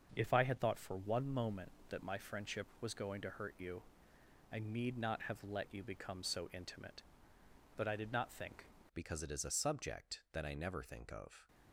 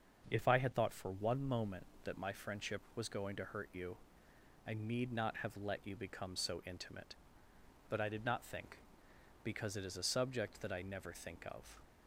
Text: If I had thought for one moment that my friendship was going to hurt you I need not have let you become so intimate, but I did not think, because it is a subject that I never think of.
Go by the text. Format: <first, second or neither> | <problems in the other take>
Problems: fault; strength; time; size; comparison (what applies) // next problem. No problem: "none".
second | starts louder than the rest; until 1.1 s; 6.5 dB; also in the second // pauses between "you" and "I"; noticeable; at 3.8 s; 0.70 s long; noticeable in the second // changes voice at "because"; from 8.9 s on; 2.5 s long